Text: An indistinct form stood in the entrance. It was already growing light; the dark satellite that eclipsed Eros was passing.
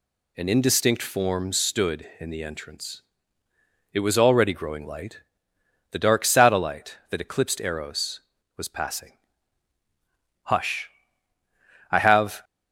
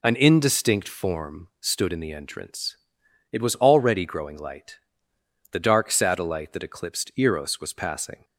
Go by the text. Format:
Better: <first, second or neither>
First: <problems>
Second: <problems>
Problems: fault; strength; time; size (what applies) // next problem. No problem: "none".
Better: second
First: goes on to say "Hush I have"; strong; from 10.4 s on; 1.9 s long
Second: none